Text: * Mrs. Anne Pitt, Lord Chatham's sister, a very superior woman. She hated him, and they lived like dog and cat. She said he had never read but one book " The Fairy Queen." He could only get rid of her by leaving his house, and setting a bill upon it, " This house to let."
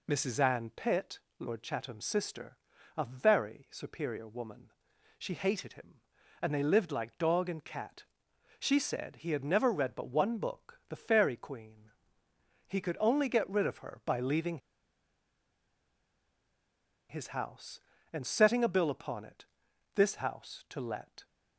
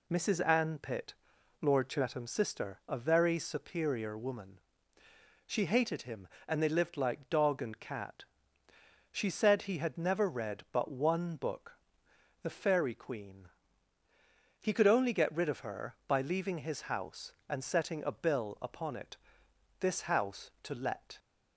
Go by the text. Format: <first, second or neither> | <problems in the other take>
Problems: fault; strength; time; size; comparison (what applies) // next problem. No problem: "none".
second | pauses between "leaving" and "his"; strong; at 14.5 s; 2.5 s long